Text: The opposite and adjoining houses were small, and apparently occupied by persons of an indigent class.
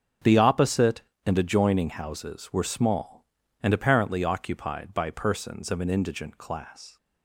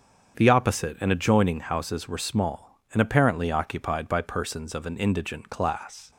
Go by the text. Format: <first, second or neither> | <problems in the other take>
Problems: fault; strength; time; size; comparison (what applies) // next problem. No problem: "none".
neither | starts louder than the rest; the same in both